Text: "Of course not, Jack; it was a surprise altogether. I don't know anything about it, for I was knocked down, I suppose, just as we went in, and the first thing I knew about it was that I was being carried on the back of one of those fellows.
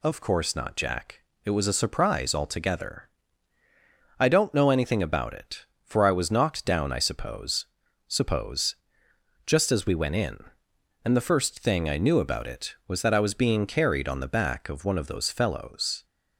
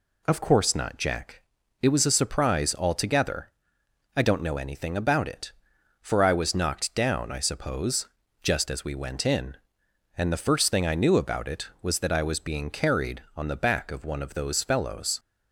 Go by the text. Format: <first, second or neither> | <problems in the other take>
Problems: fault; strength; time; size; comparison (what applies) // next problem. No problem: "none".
second | says "suppose" twice; at 8.0 s